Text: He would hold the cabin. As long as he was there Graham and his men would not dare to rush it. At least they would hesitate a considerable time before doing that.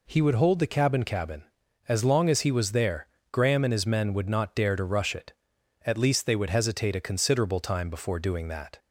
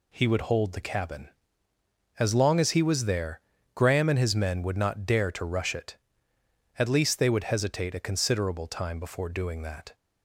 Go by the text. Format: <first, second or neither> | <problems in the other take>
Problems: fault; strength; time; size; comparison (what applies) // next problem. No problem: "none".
second | says "cabin" twice; at 1.0 s // pauses between "there" and "Graham"; slight; at 3.0 s; 0.26 s long; slight in the second